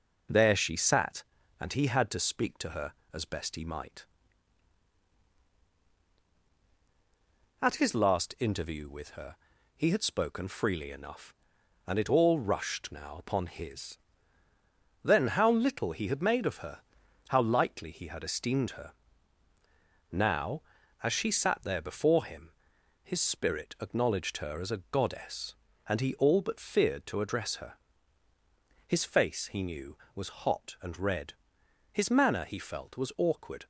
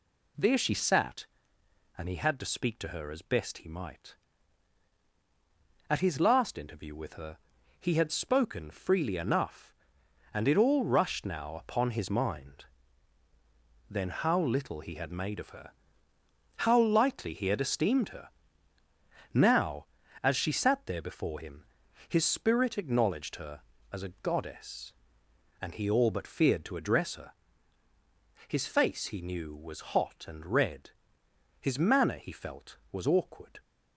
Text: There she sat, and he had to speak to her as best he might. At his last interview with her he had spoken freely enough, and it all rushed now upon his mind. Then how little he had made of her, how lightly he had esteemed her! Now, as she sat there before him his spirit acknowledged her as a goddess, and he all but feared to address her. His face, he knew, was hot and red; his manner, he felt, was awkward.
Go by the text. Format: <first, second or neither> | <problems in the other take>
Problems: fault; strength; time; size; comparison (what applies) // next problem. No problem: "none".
second | pauses between "her" and "he"; at 9.3 s; 0.42 s long; also in the second // skips "mind"; at 14.5 s // pauses between "him" and "his"; noticeable; at 22.5 s; 0.52 s long; also in the second